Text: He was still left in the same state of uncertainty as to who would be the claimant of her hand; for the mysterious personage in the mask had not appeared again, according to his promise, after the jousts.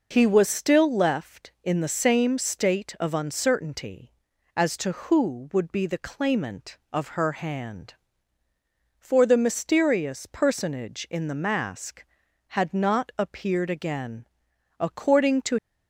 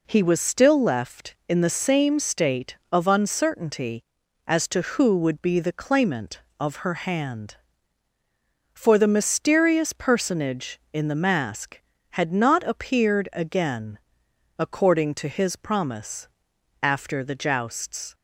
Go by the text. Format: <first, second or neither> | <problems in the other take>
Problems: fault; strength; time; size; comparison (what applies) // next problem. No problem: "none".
second | stops before "his promise after the jousts"; at 15.5 s